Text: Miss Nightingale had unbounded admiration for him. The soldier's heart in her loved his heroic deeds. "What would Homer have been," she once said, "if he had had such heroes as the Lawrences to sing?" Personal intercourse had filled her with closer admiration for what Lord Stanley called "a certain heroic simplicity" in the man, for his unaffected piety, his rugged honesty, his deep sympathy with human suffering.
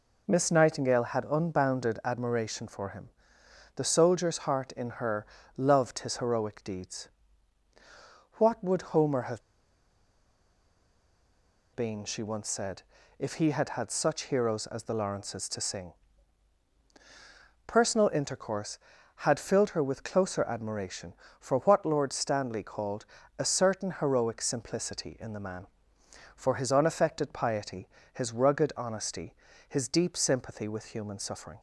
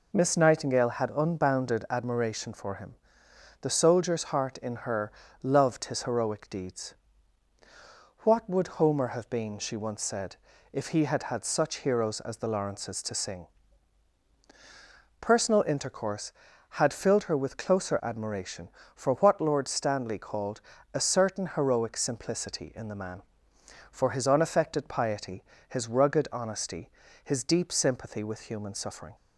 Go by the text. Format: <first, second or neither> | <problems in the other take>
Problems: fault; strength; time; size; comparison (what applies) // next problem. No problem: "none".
second | pauses between "her" and "loved"; slight; at 5.2 s; 0.30 s long; slight in the second // pauses between "have" and "been"; strong; at 9.4 s; 2.3 s long // pauses between "called" and "a"; slight; at 23.0 s; 0.32 s long; slight in the second